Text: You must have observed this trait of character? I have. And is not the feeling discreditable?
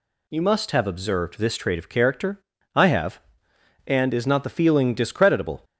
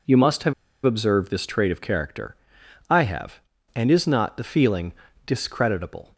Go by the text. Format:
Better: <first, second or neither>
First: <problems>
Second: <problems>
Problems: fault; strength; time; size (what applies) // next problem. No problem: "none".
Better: first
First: none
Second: pauses between "have" and "observed"; slight; at 0.5 s; 0.31 s long // pauses between "feeling" and "discreditable"; slight; at 4.9 s; 0.32 s long